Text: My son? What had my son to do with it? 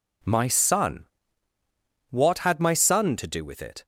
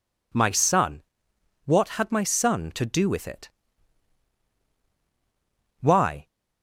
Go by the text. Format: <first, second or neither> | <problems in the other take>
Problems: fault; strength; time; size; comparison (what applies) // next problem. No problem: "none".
first | goes on to say "Why"; slight; from 5.8 s on; 0.46 s long